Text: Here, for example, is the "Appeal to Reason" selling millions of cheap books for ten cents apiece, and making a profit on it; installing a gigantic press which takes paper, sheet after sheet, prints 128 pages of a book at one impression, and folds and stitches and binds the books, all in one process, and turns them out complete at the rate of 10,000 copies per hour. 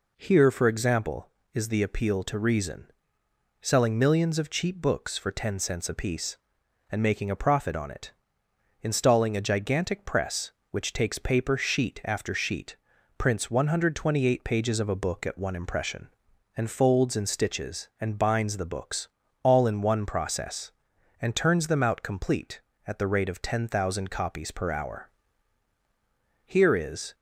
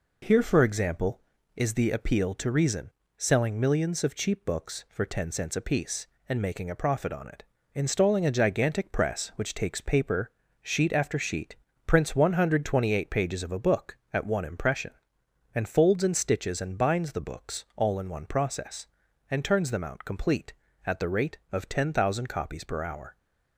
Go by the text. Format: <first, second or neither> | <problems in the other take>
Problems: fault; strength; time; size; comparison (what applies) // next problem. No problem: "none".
second | pauses between "Reason" and "selling"; noticeable; at 2.9 s; 0.70 s long; slight in the second // goes on to say "Here is"; noticeable; from 26.4 s on; 0.70 s long